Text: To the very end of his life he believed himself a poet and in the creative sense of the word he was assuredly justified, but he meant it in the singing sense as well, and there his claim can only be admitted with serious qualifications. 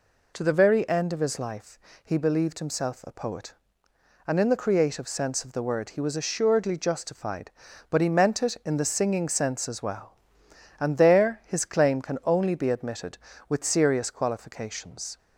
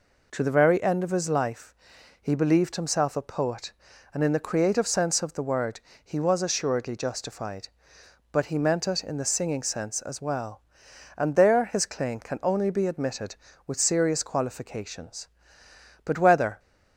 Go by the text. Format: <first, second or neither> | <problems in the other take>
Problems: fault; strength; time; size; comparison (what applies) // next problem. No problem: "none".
first | pauses between "life" and "he"; noticeable; at 1.7 s; 0.48 s long; slight in the first // pauses between "word" and "he"; slight; at 5.7 s; 0.24 s long // goes on to say "But whether"; from 16.0 s on; 0.54 s long